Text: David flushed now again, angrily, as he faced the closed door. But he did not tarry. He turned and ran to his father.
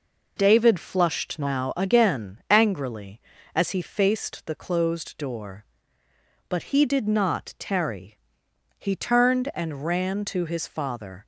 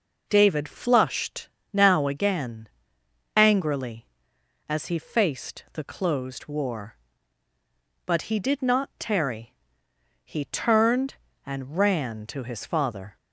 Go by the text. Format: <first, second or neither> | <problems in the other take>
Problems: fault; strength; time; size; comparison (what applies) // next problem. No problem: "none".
first | pauses between "flushed" and "now"; slight; at 1.4 s; 0.24 s long // says "war" for "door"; at 6.4 s